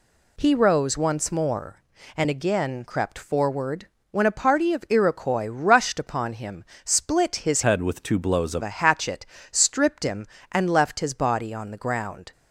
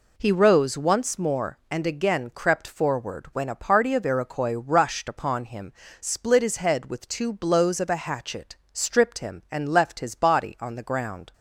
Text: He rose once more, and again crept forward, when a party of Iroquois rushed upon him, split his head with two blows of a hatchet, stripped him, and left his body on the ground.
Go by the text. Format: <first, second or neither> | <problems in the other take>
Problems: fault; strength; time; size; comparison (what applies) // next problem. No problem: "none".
second | changes voice from "head" to "of"; from 7.6 to 8.6 s; 1.0 s long